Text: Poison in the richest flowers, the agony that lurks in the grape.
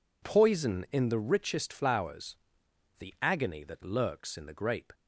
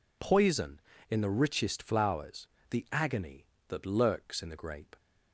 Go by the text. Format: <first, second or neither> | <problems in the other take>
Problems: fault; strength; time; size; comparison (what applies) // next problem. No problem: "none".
neither | none